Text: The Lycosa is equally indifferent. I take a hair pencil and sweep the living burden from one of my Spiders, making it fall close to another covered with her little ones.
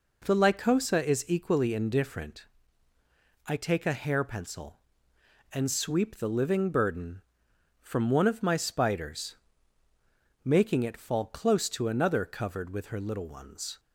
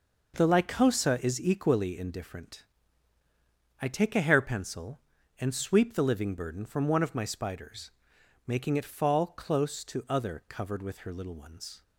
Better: first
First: none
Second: says "other" for "another"; at 10.0 s

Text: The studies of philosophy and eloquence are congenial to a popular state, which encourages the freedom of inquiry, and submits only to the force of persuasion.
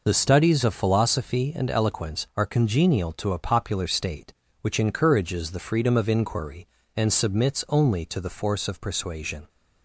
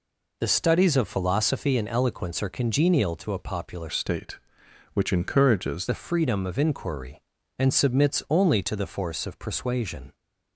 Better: first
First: none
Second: changes voice from "state" to "encourages"; from 3.8 to 5.8 s; 2.0 s long

